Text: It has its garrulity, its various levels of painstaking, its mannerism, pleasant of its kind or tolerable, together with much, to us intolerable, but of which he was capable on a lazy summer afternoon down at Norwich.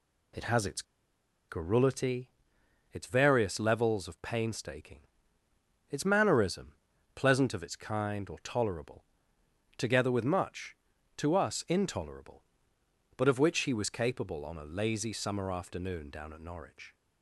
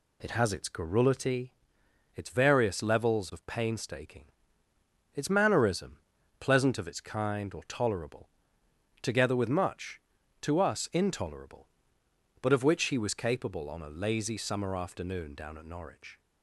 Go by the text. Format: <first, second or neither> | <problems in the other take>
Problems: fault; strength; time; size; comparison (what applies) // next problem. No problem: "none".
second | pauses between "its" and "garrulity"; noticeable; at 0.8 s; 0.66 s long